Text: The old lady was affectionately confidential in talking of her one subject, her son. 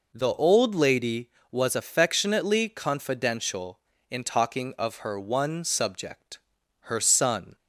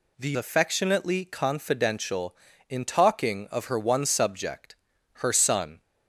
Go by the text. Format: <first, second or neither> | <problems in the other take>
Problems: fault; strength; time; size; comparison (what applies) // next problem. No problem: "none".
first | skips "old lady was"; at 0.3 s